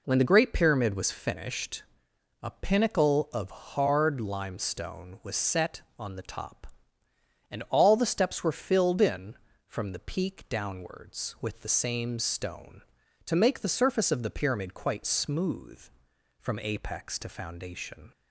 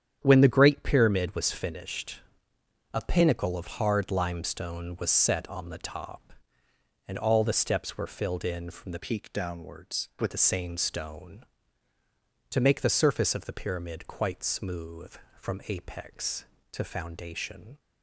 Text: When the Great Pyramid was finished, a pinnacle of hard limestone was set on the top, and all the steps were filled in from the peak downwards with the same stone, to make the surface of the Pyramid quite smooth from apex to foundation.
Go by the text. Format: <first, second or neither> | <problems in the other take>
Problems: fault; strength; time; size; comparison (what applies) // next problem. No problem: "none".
first | starts louder than the rest; strong; until 1.2 s; 9 dB // changes voice from "peak" to "with"; from 8.9 to 10.3 s; 1.4 s long